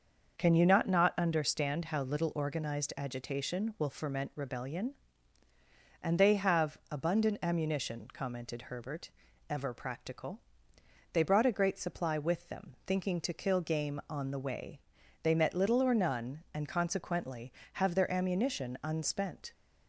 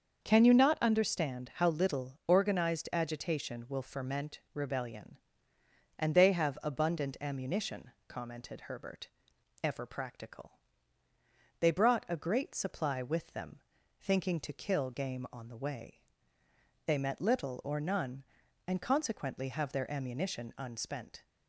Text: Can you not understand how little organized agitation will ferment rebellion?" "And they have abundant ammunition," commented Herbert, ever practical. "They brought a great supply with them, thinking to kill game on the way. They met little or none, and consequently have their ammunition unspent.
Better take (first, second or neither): second